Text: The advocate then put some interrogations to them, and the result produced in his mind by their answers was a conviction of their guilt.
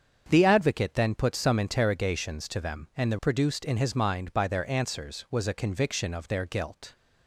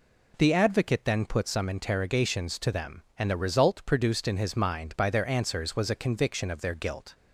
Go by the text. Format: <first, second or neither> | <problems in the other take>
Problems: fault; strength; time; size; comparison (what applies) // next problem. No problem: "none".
second | starts louder than the rest; strong; until 1.2 s; 7.5 dB // skips "result"; at 3.1 s